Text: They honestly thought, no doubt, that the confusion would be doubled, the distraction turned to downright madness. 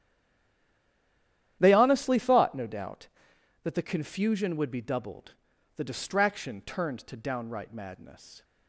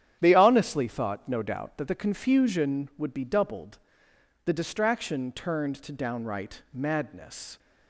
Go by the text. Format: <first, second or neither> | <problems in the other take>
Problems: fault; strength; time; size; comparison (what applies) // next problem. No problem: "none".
second | stays silent before the first word; noticeable; until 1.6 s; 1.6 s long // starts louder than the rest; strong; until 2.6 s; 11 dB; strong in the second